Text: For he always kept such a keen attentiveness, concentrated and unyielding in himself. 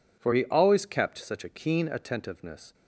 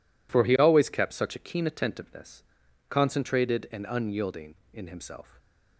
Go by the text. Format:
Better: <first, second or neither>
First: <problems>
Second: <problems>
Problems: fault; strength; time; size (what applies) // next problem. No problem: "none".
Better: second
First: stops before "concentrated and unyielding in himself"; at 2.7 s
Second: none